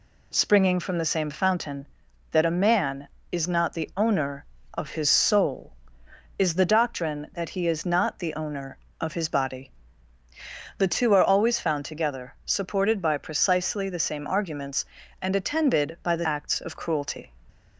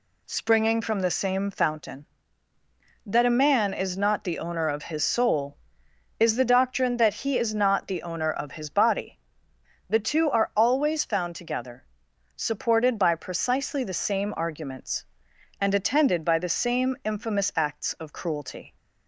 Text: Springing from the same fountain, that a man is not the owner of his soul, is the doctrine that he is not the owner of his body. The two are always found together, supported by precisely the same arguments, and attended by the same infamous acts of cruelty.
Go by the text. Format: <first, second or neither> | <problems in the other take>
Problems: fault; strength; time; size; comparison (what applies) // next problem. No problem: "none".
second | skips "same infamous"; at 16.2 s